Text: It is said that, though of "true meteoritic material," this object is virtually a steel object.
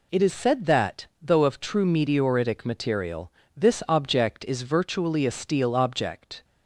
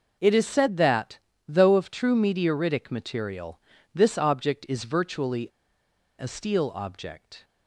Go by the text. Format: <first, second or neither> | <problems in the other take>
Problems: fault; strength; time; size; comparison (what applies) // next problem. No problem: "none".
first | pauses between "virtually" and "a"; noticeable; at 5.4 s; 0.70 s long